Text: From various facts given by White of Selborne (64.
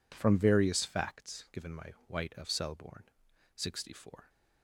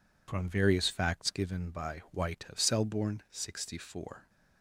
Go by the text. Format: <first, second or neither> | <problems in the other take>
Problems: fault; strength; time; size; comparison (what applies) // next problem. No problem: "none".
second | says "my" for "by"; at 1.7 s